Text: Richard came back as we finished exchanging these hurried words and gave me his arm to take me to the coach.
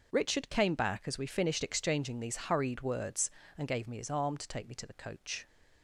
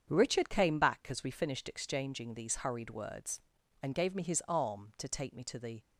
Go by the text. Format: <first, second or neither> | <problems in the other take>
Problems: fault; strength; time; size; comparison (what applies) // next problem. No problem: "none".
first | starts louder than the rest; strong; until 1.1 s; 7.5 dB // stops before "coach"; at 5.8 s